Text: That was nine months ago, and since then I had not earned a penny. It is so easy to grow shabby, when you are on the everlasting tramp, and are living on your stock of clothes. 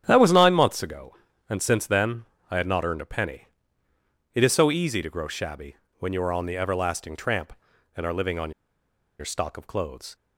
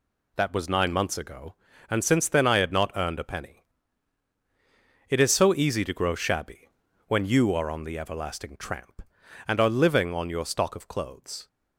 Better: second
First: starts louder than the rest; strong; until 1.0 s; 9.5 dB // pauses between "then" and "I"; slight; at 2.2 s; 0.26 s long // pauses between "on" and "your"; noticeable; at 8.5 s; 0.68 s long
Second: none

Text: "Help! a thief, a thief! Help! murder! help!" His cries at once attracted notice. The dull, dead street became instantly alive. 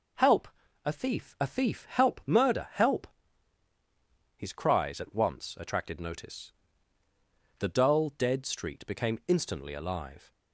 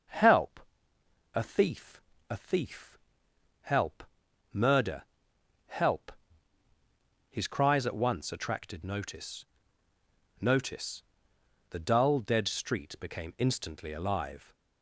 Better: first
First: none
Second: starts louder than the rest; until 1.8 s; 6.5 dB // says "notice" twice; at 10.4 s

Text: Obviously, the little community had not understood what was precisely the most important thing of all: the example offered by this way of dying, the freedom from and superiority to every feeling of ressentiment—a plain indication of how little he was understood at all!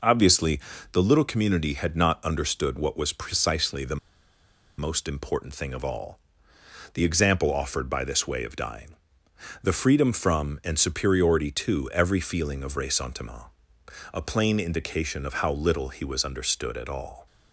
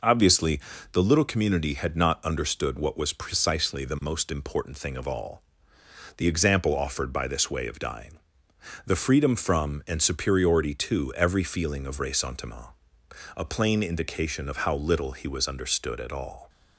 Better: second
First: pauses between "the" and "most"; noticeable; at 3.9 s; 0.81 s long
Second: none

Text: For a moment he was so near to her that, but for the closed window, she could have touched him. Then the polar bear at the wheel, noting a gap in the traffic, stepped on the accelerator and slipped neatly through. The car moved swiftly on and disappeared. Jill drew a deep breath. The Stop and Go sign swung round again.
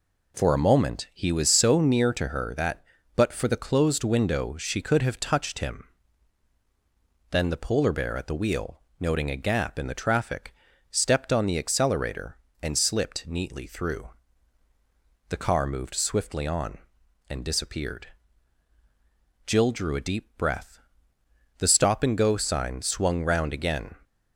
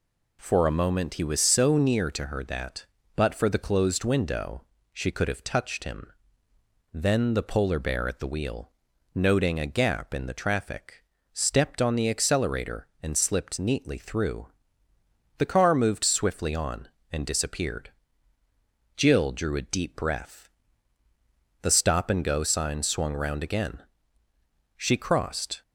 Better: first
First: none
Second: goes on to say "She crossed"; noticeable; from 24.7 s on; 0.84 s long

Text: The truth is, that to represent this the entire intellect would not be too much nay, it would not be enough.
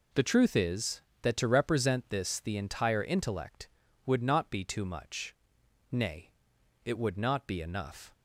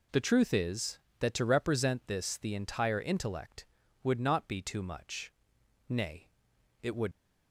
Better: first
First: pauses between "much" and "nay"; noticeable; at 5.3 s; 0.56 s long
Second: pauses between "much" and "nay"; noticeable; at 5.3 s; 0.56 s long // stops before "not be enough"; at 7.1 s

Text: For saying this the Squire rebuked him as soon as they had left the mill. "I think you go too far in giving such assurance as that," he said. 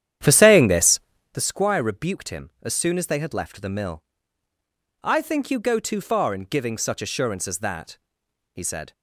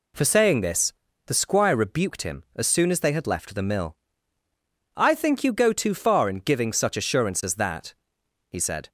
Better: second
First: starts louder than the rest; strong; until 1.4 s; 10.5 dB // pauses between "this" and "the"; slight; at 0.9 s; 0.32 s long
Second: pauses between "this" and "the"; slight; at 0.9 s; 0.32 s long

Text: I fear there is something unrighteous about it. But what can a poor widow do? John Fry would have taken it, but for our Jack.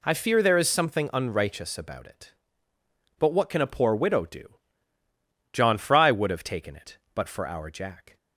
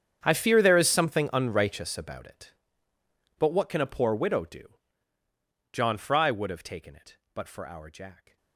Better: first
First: none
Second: gets quieter; strong; throughout; 20.5 dB

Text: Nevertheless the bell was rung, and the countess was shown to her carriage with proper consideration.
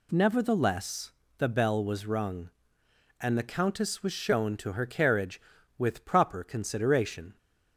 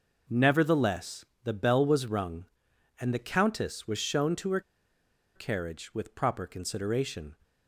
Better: first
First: pauses between "Nevertheless" and "the"; slight; at 1.1 s; 0.24 s long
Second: pauses between "Nevertheless" and "the"; slight; at 1.2 s; 0.20 s long // pauses between "her" and "carriage"; noticeable; at 4.6 s; 0.74 s long

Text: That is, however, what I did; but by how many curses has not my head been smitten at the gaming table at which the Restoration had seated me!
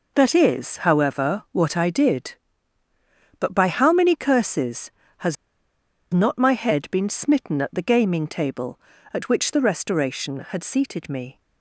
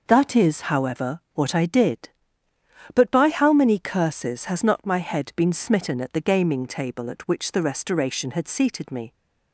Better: second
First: pauses between "has" and "not"; noticeable; at 5.3 s; 0.76 s long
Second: none

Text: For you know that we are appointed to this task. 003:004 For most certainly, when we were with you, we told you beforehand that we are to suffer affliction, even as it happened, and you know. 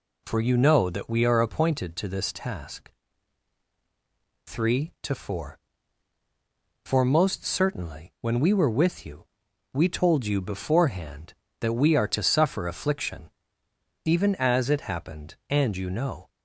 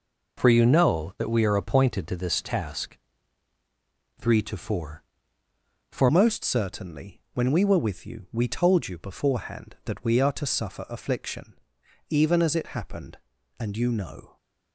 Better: first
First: none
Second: changes voice at "most"; from 6.1 s on; 8.2 s long

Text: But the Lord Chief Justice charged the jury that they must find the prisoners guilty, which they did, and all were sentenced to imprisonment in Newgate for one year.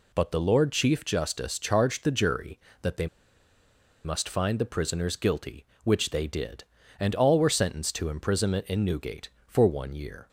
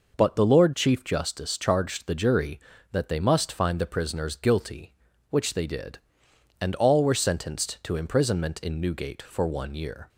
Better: second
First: pauses between "they" and "must"; at 3.0 s; 0.98 s long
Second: none

